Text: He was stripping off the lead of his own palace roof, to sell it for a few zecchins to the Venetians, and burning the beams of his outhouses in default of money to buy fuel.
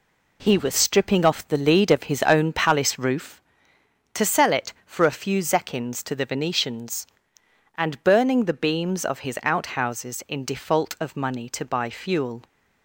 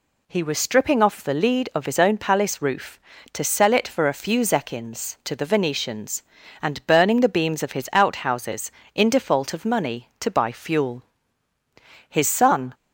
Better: first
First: none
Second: goes on to say "His son"; noticeable; from 12.0 s on; 0.64 s long

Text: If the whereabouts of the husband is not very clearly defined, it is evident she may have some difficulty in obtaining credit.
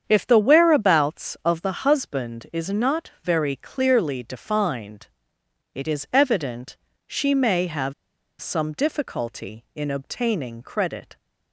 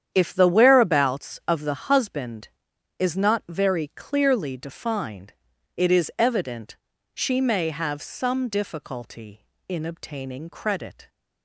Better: second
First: starts louder than the rest; strong; until 1.0 s; 8 dB // pauses between "evident" and "she"; slight; at 6.7 s; 0.30 s long // pauses between "have" and "some"; noticeable; at 7.9 s; 0.48 s long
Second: starts louder than the rest; strong; until 1.1 s; 9 dB // pauses between "evident" and "she"; at 6.7 s; 0.36 s long

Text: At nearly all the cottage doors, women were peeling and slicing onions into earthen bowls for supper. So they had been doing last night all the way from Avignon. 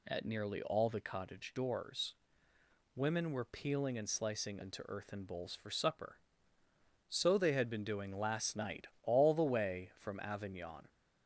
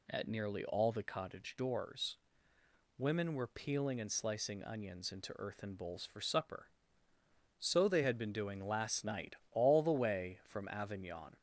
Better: second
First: skips "onions"; at 4.6 s // pauses between "night" and "all"; slight; at 8.8 s; 0.18 s long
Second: pauses between "night" and "all"; slight; at 9.3 s; 0.18 s long

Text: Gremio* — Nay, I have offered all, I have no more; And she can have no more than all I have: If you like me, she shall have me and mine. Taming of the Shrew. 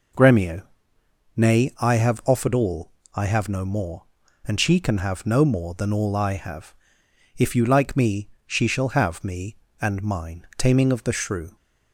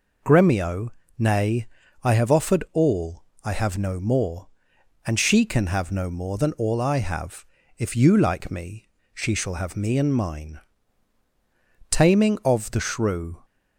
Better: neither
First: none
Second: none

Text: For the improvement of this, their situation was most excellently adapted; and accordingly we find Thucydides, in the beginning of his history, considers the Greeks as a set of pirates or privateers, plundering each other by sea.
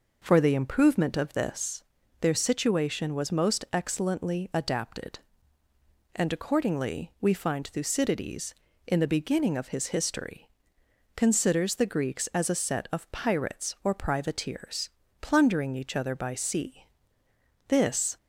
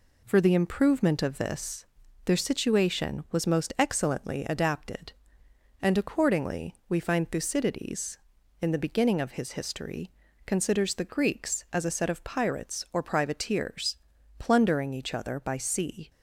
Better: second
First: goes on to say "This"; from 17.6 s on; 0.50 s long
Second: none

